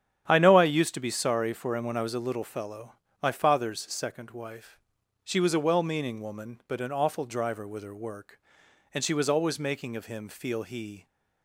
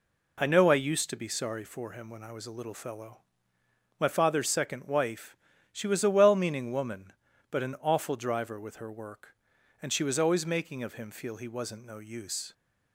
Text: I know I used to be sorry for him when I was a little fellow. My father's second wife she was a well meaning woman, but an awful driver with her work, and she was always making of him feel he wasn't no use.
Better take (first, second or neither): second